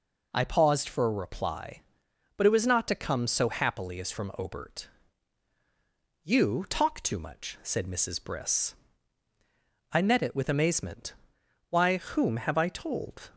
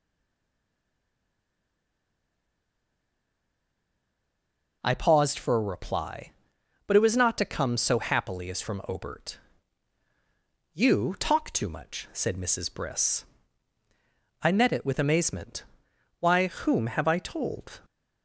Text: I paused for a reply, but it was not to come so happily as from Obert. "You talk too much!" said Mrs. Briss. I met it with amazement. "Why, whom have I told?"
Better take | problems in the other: first | stays silent before the first word; strong; until 4.8 s; 4.8 s long

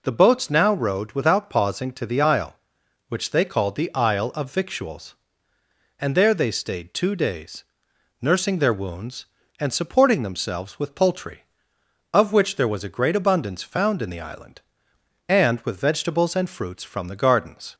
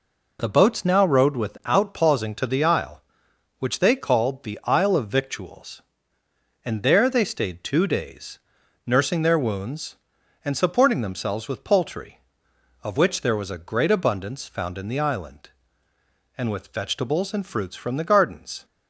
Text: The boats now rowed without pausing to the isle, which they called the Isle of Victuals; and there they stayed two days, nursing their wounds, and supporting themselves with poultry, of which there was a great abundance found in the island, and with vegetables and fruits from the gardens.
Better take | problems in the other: neither | none

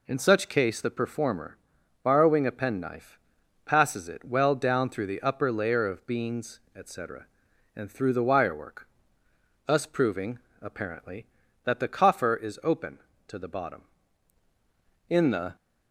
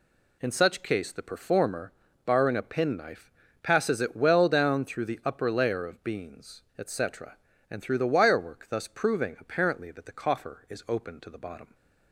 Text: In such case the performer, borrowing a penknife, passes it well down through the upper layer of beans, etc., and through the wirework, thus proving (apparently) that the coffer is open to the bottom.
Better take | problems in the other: second | goes on to say "In the"; slight; from 15.0 s on; 0.46 s long

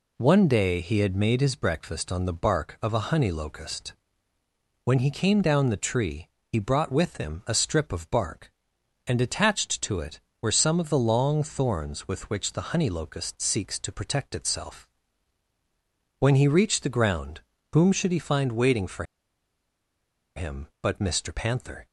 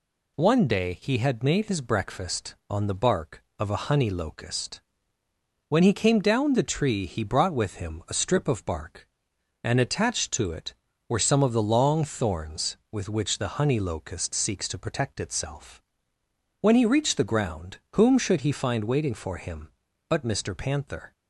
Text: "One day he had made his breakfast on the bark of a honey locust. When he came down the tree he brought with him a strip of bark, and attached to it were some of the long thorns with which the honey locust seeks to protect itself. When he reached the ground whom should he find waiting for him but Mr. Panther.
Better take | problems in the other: second | pauses between "tree" and "he"; slight; at 6.2 s; 0.18 s long // pauses between "ground" and "whom"; slight; at 17.4 s; 0.32 s long; slight in the second // pauses between "for" and "him"; strong; at 19.0 s; 1.3 s long

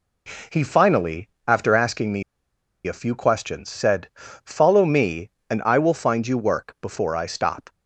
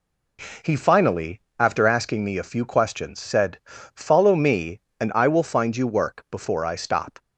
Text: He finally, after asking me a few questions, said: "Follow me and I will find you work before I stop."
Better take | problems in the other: second | pauses between "me" and "a"; noticeable; at 2.2 s; 0.63 s long

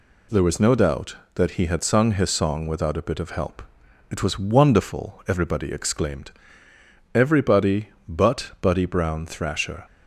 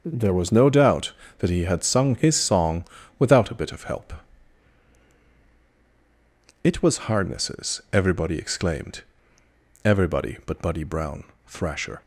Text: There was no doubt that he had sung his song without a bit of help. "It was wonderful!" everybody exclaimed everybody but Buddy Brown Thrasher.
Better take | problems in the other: first | starts louder than the rest; until 1.0 s; 6.5 dB // pauses between "song" and "without"; slight; at 2.8 s; 0.32 s long // says "hardnesses" for "wonderful"; at 7.0 s // pauses between "exclaimed" and "everybody"; noticeable; at 9.0 s; 0.82 s long; noticeable in the first // pauses between "Brown" and "Thrasher"; slight; at 11.2 s; 0.24 s long

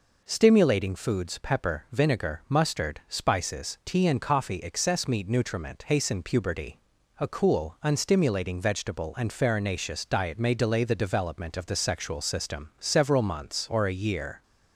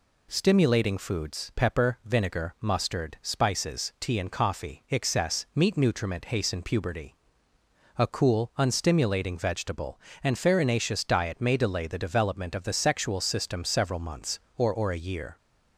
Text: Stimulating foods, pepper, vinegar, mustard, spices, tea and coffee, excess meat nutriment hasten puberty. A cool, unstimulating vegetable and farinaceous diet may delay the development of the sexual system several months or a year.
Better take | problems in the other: first | says "or" twice; at 14.6 s

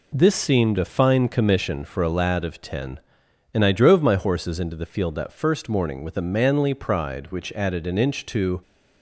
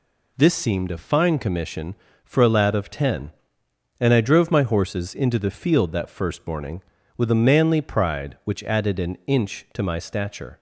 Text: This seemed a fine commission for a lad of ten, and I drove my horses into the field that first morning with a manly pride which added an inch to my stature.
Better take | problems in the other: second | stops before "my stature"; at 8.6 s

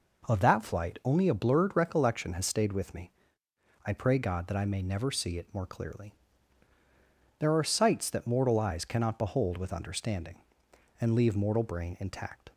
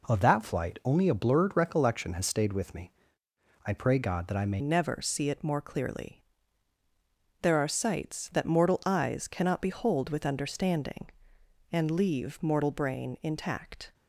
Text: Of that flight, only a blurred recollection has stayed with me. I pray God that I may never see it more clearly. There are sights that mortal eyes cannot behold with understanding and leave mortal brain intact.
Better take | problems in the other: first | changes voice at "never"; from 4.5 s on; 9.4 s long

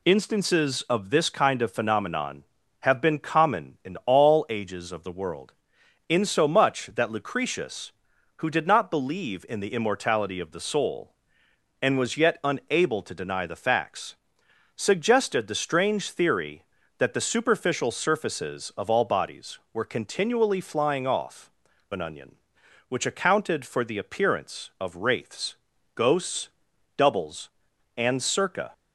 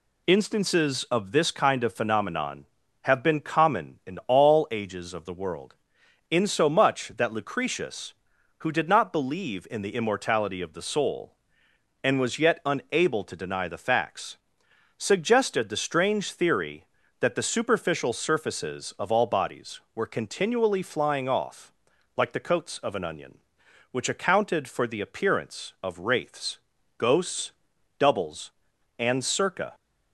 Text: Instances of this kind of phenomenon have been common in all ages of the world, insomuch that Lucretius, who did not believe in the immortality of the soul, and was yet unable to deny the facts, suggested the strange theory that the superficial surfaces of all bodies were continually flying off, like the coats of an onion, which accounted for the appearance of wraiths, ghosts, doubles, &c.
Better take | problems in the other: second | skips "like the coats of"; at 21.7 s

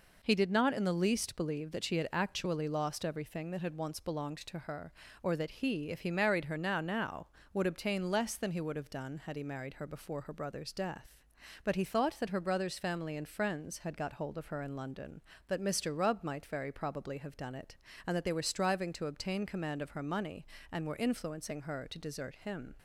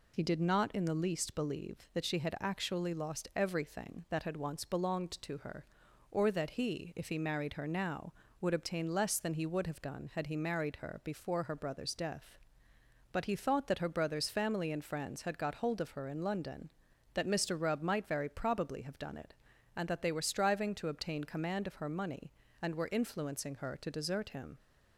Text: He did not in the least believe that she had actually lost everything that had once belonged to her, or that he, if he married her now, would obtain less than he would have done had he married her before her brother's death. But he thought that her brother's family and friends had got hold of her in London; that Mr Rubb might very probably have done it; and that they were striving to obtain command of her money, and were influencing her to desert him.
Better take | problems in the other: second | says "now" twice; at 6.7 s

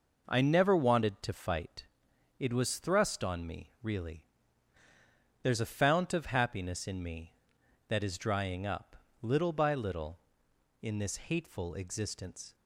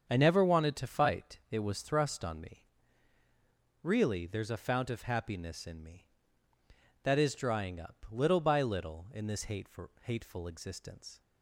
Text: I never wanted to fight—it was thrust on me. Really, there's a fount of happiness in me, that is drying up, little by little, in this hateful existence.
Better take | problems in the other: first | starts louder than the rest; strong; until 1.1 s; 7.5 dB // says "hateful" twice; at 10.0 s

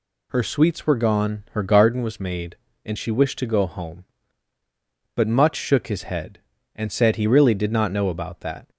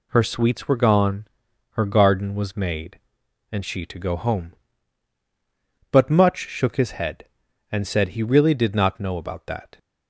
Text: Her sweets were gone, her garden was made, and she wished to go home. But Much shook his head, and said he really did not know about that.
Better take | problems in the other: first | skips "wished"; at 3.8 s

